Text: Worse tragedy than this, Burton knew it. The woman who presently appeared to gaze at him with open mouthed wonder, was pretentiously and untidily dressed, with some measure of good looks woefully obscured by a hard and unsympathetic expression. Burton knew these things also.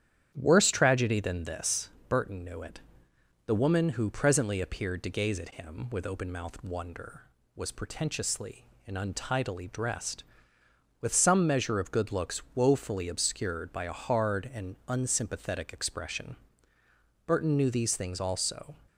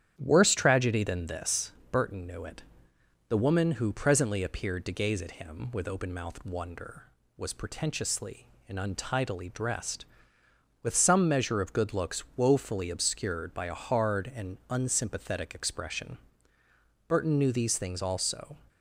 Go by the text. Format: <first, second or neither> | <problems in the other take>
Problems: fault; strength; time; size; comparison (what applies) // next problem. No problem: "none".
neither | starts louder than the rest; strong; the same in both